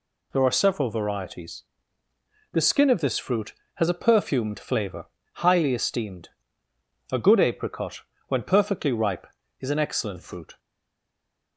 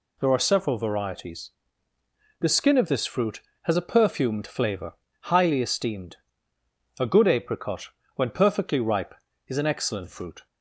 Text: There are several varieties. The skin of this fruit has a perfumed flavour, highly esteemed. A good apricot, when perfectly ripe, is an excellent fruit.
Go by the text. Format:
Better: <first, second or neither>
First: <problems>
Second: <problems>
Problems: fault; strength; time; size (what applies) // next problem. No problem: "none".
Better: second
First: stays silent after the last word; from 10.5 s on; 1.0 s long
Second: none